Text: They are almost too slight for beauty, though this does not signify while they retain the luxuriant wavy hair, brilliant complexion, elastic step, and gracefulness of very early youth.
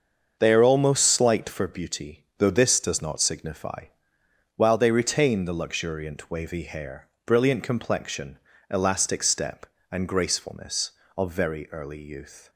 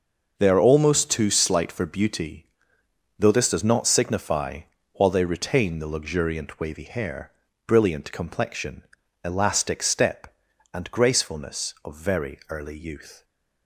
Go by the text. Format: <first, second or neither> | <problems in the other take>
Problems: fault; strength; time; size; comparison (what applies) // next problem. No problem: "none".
second | starts louder than the rest; until 1.4 s; 6.5 dB // skips "too"; at 1.0 s // pauses between "signify" and "while"; noticeable; at 3.8 s; 0.70 s long; slight in the second